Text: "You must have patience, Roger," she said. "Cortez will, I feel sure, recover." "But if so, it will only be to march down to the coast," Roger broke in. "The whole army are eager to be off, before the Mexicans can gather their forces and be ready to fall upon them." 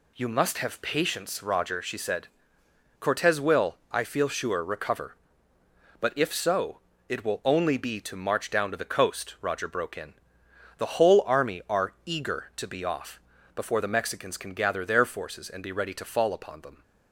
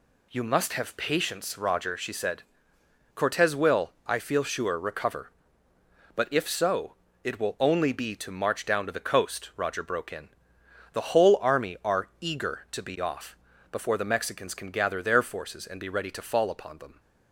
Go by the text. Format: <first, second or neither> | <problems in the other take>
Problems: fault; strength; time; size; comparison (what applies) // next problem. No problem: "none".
neither | none